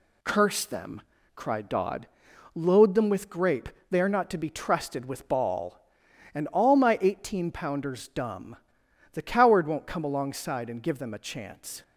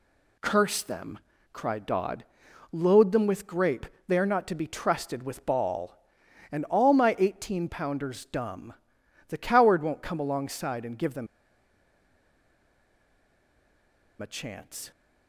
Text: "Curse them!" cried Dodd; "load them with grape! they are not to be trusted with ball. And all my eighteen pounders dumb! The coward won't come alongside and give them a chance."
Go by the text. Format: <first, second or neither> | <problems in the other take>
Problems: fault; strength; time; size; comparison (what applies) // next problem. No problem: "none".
first | pauses between "them" and "a"; strong; at 11.2 s; 2.9 s long